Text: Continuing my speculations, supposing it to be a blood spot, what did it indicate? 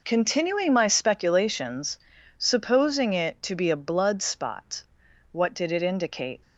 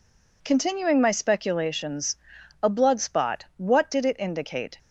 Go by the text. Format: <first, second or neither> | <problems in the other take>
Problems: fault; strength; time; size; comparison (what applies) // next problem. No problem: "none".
first | skips "supposing it to be"; at 2.3 s